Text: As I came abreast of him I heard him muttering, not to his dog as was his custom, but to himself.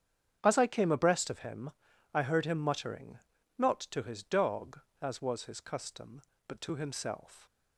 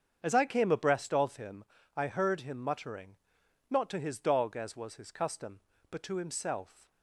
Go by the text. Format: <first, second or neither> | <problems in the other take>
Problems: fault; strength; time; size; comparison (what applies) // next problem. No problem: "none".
neither | starts louder than the rest; strong; the same in both // pauses between "him" and "I"; the same in both